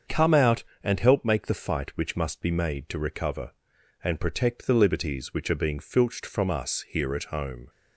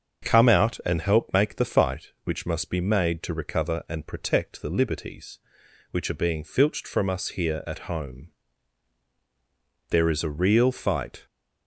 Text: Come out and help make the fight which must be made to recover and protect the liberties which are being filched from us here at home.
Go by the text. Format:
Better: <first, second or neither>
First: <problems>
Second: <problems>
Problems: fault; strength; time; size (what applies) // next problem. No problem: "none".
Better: first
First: starts louder than the rest; until 1.2 s; 7 dB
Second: starts louder than the rest; until 1.3 s; 6.5 dB // goes on to say "There is a real fight"; from 9.8 s on; 1.3 s long